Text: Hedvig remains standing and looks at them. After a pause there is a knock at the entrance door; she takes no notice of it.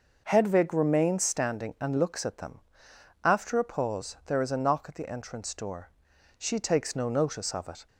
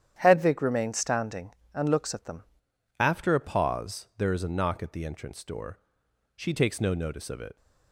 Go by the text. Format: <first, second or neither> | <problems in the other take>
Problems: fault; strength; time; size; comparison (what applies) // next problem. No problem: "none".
first | starts louder than the rest; strong; until 1.2 s; 10 dB // changes voice at "After"; from 2.9 s on; 4.6 s long